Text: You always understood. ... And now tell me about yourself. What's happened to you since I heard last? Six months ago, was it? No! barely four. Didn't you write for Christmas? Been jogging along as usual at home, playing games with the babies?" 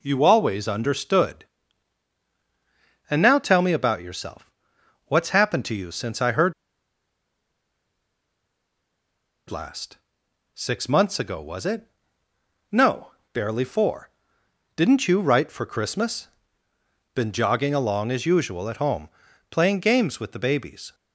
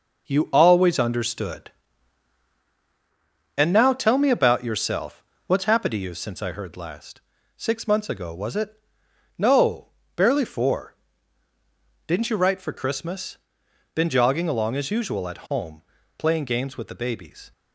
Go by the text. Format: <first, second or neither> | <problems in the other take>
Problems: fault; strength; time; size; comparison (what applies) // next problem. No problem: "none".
second | pauses between "heard" and "last"; strong; at 6.5 s; 2.9 s long